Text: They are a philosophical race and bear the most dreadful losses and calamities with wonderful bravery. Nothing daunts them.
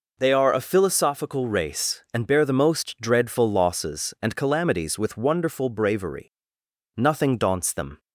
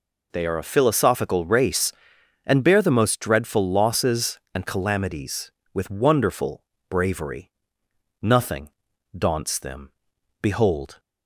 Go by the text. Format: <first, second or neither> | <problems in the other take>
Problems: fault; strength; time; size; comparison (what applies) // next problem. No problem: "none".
first | pauses between "wonderful" and "bravery"; slight; at 6.6 s; 0.26 s long // pauses between "Nothing" and "daunts"; noticeable; at 8.6 s; 0.48 s long // goes on to say "Behold"; from 10.4 s on; 0.58 s long